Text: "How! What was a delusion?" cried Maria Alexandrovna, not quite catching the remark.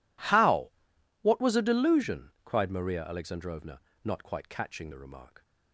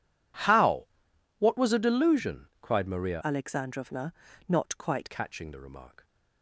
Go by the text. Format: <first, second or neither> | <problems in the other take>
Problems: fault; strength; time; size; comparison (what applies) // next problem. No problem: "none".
first | changes voice from "Alexandrovna" to "quite"; from 3.2 to 5.1 s; 1.9 s long